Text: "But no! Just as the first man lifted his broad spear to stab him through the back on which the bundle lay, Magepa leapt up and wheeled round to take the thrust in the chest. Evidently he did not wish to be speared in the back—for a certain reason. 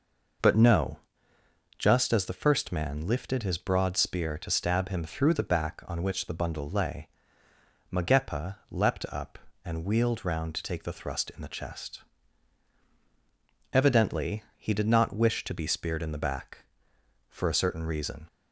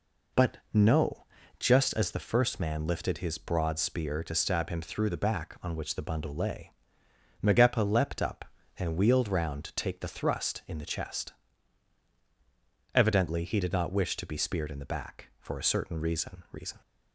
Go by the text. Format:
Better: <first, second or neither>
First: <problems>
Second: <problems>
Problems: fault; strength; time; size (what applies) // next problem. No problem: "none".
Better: first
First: none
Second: says "reason" twice; at 16.5 s